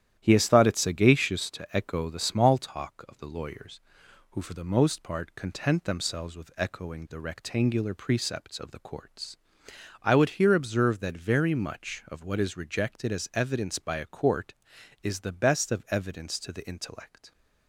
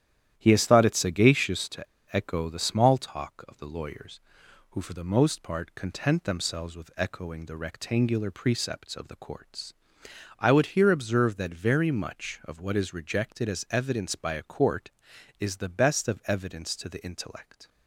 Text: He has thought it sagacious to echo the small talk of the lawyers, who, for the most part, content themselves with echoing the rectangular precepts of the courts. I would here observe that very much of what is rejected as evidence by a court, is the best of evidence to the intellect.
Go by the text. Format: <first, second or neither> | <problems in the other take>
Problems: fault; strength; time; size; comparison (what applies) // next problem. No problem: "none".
first | starts louder than the rest; strong; until 1.4 s; 11 dB; strong in the first // pauses between "to" and "echo"; slight; at 1.8 s; 0.29 s long